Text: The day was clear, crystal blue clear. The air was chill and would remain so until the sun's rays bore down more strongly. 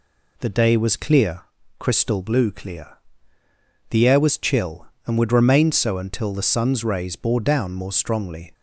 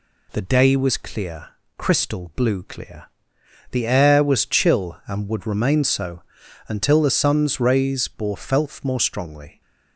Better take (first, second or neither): first